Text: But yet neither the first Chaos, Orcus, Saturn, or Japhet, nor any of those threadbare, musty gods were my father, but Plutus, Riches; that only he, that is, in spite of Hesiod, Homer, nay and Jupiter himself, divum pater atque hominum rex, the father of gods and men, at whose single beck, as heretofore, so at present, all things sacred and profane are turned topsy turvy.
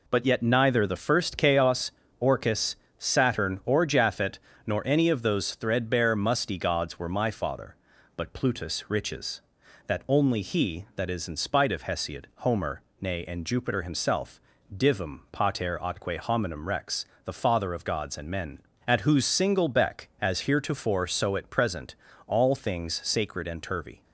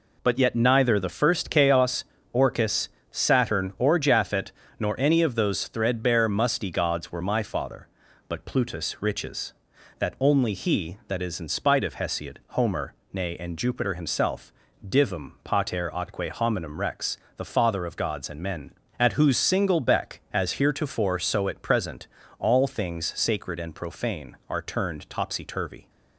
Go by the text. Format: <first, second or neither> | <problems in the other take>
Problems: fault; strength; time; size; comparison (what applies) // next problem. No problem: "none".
second | skips "profane are turned topsy"; at 23.6 s